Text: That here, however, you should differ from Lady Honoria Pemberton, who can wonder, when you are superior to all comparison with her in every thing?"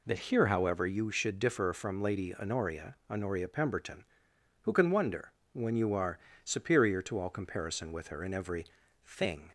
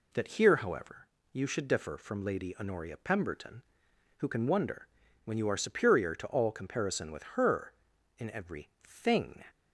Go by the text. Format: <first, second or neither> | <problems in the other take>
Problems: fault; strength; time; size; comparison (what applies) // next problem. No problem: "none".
second | says "Honoria" twice; at 3.0 s // pauses between "are" and "superior"; slight; at 6.1 s; 0.24 s long // pauses between "every" and "thing"; at 8.6 s; 0.40 s long